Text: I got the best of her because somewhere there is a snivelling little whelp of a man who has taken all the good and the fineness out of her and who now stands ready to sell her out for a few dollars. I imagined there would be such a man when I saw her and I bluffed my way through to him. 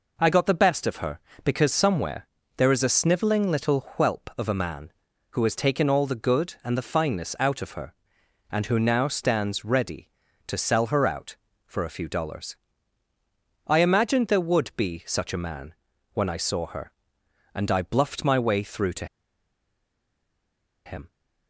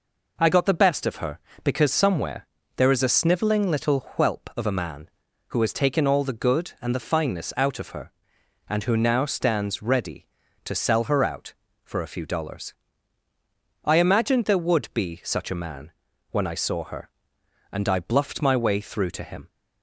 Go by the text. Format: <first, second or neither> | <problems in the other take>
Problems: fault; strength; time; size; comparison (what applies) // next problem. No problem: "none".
second | pauses between "somewhere" and "there"; slight; at 2.2 s; 0.30 s long; slight in the second // pauses between "man" and "when"; at 15.7 s; 0.40 s long; also in the second // pauses between "to" and "him"; strong; at 19.0 s; 1.8 s long